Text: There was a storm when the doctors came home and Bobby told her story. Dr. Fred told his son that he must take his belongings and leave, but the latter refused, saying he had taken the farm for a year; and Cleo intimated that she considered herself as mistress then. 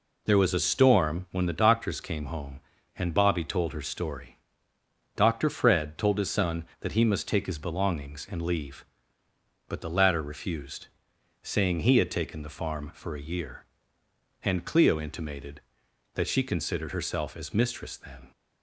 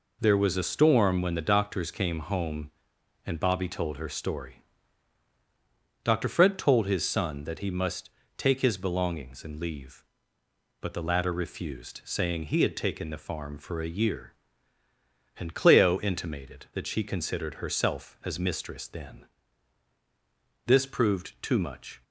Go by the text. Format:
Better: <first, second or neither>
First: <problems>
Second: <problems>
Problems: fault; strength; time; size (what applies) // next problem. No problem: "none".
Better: first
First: none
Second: pauses between "must" and "take"; slight; at 8.0 s; 0.28 s long // goes on to say "This proved too much"; from 20.6 s on; 1.3 s long